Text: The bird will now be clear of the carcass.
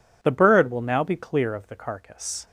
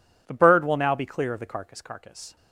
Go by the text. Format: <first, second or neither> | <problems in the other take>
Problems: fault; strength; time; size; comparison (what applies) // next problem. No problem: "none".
first | says "carcass" twice; at 1.8 s